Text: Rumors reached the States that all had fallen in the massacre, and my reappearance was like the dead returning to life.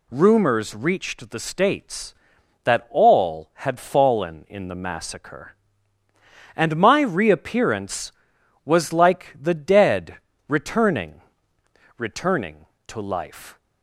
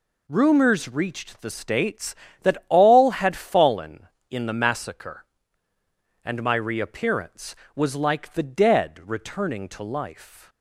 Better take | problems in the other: second | pauses between "dead" and "returning"; slight; at 10.1 s; 0.30 s long // says "returning" twice; at 11.9 s

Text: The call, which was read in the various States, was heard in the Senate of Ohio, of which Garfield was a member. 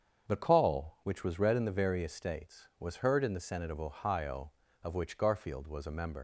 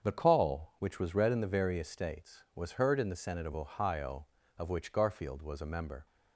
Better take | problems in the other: second | starts louder than the rest; until 1.3 s; 7 dB; strong in the second // leaves "member" unfinished; at 6.1 s; 75 ms

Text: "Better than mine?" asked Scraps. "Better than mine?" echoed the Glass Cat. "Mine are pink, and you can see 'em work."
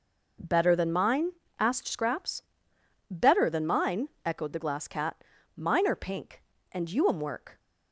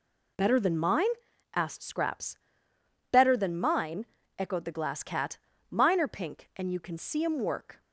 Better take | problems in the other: second | skips "can see"; at 7.0 s

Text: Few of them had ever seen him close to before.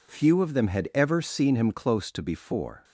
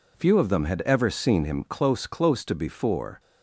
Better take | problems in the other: first | says "close" twice; at 2.0 s

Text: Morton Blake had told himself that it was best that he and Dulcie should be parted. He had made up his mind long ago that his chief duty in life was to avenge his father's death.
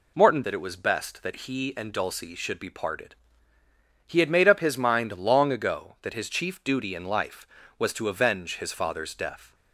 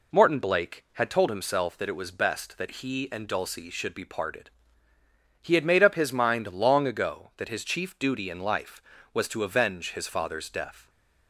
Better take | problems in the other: second | skips "Blake had told himself"; at 0.4 s

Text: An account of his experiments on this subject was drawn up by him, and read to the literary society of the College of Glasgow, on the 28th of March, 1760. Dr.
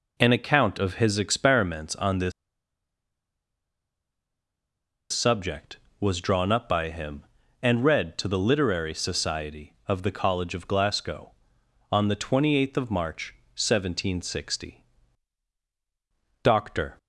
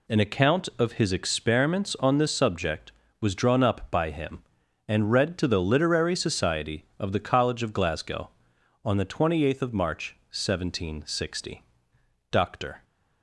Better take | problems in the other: second | pauses between "this" and "subject"; strong; at 2.3 s; 2.8 s long

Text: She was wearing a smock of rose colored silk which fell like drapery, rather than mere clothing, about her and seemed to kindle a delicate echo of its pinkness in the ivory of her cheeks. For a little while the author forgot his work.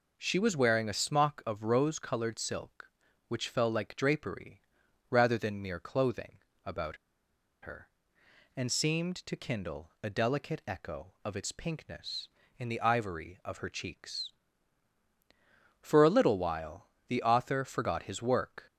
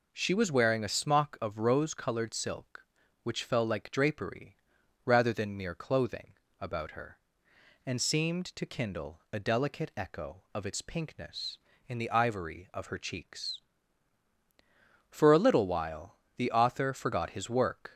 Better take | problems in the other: second | pauses between "about" and "her"; noticeable; at 6.9 s; 0.65 s long // pauses between "while" and "the"; slight; at 16.8 s; 0.20 s long; slight in the second

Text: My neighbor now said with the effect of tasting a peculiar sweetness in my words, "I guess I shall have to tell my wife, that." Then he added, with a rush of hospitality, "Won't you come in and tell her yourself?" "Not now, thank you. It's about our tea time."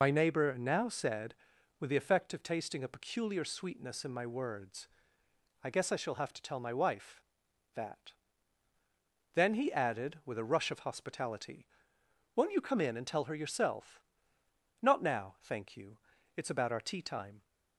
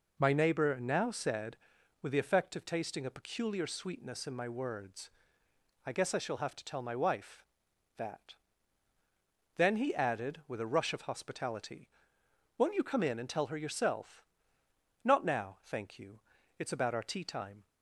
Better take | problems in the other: second | loses the start of "My"; at 0.0 s; 40 ms

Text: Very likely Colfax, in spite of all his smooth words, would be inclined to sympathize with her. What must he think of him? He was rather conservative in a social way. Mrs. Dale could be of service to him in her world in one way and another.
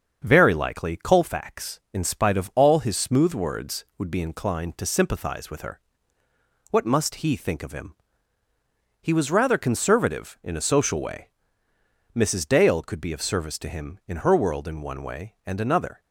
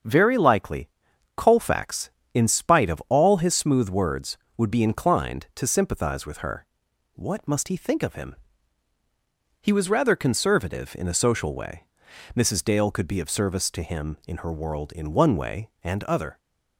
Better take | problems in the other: first | starts louder than the rest; until 1.5 s; 7 dB; also in the first // pauses between "likely" and "Colfax"; noticeable; at 0.8 s; 0.46 s long // says "other" for "another"; at 16.0 s

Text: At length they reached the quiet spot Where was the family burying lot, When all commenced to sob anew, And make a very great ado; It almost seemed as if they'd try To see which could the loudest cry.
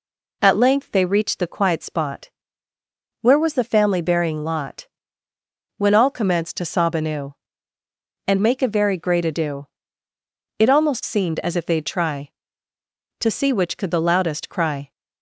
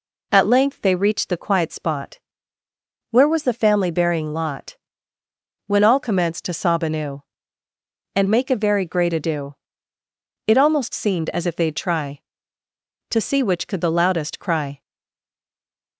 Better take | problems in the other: first | pauses between "spot" and "Where"; noticeable; at 2.1 s; 0.92 s long; noticeable in the first // stays silent after the last word; noticeable; from 14.8 s on; 1.1 s long

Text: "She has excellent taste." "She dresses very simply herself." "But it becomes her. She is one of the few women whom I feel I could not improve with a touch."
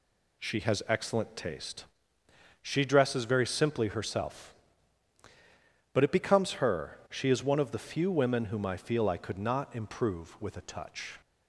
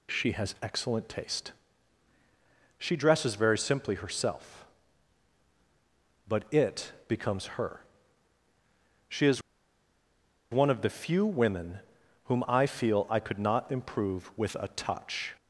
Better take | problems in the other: first | pauses between "it" and "becomes"; slight; at 6.9 s; 0.16 s long // pauses between "is" and "one"; at 9.4 s; 1.1 s long // pauses between "women" and "whom"; at 11.7 s; 0.44 s long

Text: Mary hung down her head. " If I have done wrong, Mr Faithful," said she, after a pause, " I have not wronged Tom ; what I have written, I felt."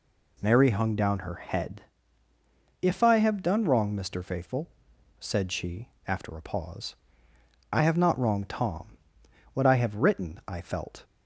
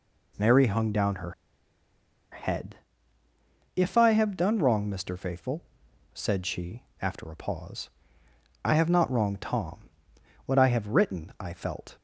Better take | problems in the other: first | pauses between "her" and "head"; at 1.3 s; 0.99 s long

